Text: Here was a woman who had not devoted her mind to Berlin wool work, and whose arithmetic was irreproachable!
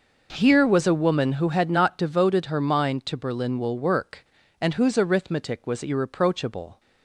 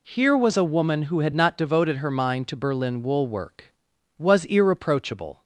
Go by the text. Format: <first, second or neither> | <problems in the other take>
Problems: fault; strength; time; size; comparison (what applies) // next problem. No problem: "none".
first | skips "and whose arithmetic"; at 3.9 s